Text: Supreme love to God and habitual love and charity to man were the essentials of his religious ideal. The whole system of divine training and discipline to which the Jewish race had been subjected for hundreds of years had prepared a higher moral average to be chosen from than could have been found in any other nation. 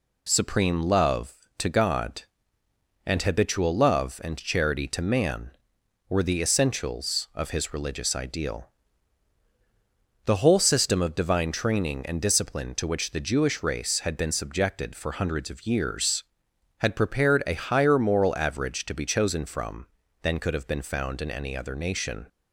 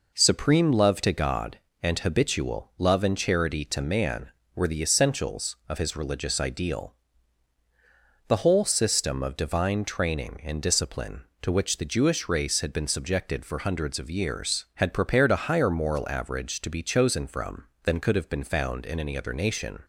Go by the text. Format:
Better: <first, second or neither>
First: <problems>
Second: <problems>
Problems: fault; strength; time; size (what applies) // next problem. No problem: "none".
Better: neither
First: none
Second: none